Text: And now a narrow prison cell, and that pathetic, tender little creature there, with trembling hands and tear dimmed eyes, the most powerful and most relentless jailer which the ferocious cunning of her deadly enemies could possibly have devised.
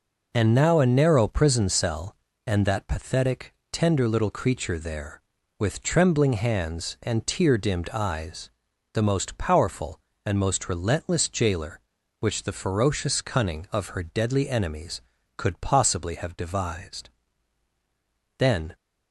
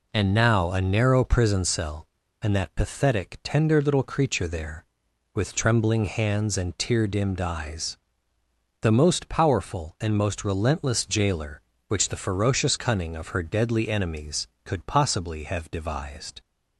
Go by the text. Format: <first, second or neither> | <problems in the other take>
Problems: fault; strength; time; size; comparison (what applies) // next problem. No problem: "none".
second | goes on to say "Then"; slight; from 18.3 s on; 0.36 s long